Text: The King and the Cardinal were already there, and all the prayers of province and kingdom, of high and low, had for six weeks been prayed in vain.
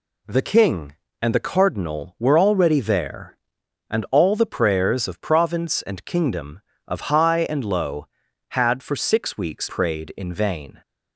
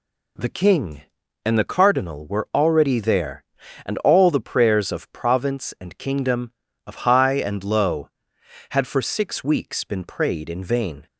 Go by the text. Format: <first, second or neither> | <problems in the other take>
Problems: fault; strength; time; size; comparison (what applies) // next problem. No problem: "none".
second | skips "been"; at 9.6 s